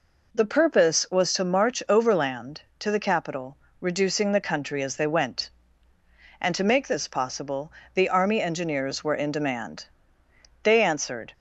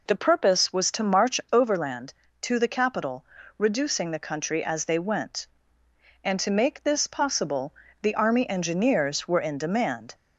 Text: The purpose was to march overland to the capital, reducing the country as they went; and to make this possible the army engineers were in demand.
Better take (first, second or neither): second